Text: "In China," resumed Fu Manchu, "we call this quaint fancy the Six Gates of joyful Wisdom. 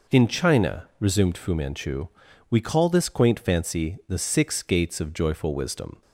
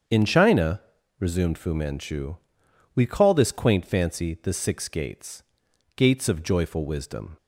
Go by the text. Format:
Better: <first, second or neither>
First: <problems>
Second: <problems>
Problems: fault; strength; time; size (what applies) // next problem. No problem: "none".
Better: first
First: none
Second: starts louder than the rest; strong; until 1.4 s; 7.5 dB // says "Gates" twice; at 5.9 s